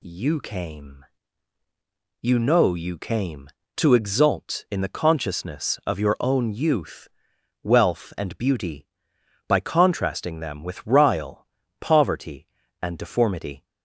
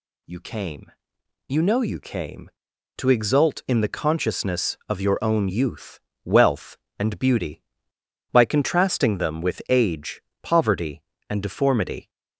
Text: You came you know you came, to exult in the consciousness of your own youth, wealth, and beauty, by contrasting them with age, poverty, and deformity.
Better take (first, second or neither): second